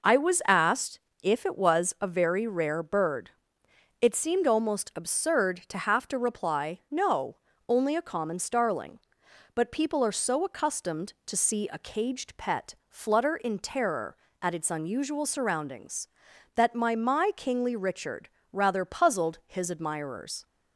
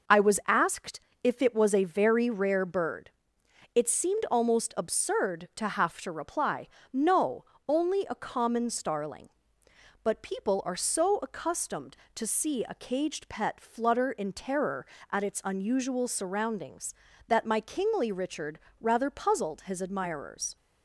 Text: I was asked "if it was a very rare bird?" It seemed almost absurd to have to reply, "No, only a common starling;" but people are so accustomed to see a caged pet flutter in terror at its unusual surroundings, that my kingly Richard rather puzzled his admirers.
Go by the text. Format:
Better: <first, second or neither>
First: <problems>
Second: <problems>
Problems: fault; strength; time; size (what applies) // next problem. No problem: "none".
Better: second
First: pauses between "asked" and "if"; slight; at 0.9 s; 0.22 s long // says "my" twice; at 16.9 s // pauses between "Richard" and "rather"; slight; at 18.2 s; 0.24 s long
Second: pauses between "asked" and "if"; slight; at 0.9 s; 0.24 s long // pauses between "Richard" and "rather"; slight; at 18.5 s; 0.20 s long